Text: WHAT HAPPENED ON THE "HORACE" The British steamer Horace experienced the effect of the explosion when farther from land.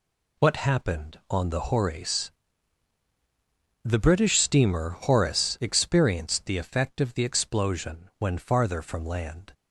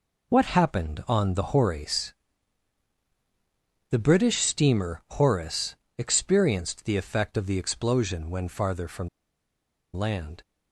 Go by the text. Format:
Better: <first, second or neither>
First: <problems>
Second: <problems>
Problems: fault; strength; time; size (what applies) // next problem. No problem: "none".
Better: first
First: pauses between "HORACE" and "The"; strong; at 2.2 s; 1.5 s long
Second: pauses between "HORACE" and "The"; strong; at 2.1 s; 1.7 s long // pauses between "Horace" and "experienced"; slight; at 5.7 s; 0.22 s long // pauses between "from" and "land"; noticeable; at 9.0 s; 0.85 s long